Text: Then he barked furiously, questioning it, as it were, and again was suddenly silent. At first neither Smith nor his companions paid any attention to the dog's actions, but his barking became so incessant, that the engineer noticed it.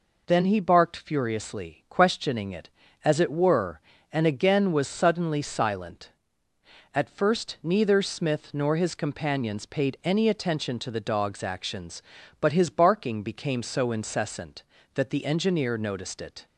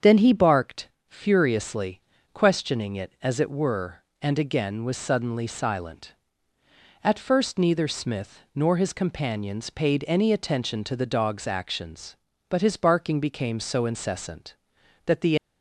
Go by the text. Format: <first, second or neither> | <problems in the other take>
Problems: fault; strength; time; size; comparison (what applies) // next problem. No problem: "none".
first | starts louder than the rest; strong; until 1.2 s; 7 dB // pauses between "barked" and "furiously"; slight; at 0.8 s; 0.20 s long // stops before "engineer noticed it"; at 15.3 s